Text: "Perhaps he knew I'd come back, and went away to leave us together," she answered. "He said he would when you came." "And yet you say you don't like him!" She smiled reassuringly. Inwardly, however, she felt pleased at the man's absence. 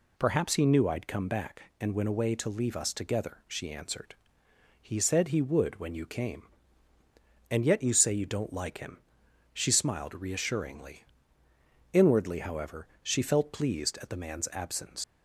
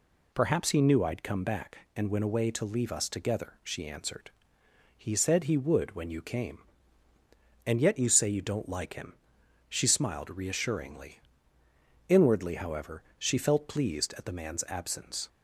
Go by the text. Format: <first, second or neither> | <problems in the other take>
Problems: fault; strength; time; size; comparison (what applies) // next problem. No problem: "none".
second | leaves "absence" unfinished; at 15.0 s; 85 ms